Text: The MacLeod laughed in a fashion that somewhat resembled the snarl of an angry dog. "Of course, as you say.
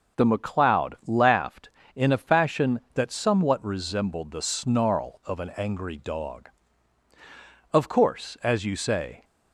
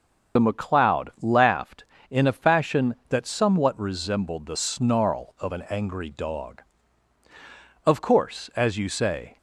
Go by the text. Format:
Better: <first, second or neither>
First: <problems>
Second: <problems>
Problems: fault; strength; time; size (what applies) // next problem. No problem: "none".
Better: first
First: starts louder than the rest; until 1.2 s; 6 dB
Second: loses the start of "The"; at 0.3 s; 40 ms // starts louder than the rest; until 1.4 s; 7 dB